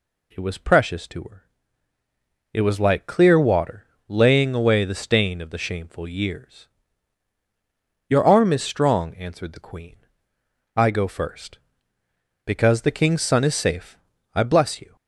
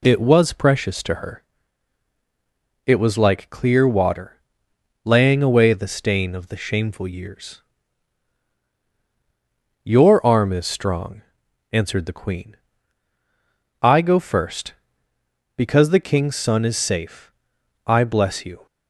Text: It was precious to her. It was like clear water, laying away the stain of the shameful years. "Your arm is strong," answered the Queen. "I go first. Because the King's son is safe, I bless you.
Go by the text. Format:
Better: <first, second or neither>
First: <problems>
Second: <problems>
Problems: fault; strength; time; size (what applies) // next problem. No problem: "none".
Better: neither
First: none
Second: none